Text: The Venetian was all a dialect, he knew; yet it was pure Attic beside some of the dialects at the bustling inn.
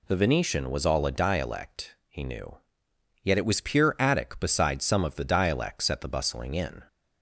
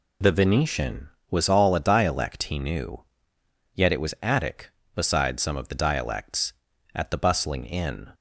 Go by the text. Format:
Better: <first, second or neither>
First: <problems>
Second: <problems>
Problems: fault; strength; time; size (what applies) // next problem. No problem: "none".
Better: first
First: none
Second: skips "pure"; at 4.1 s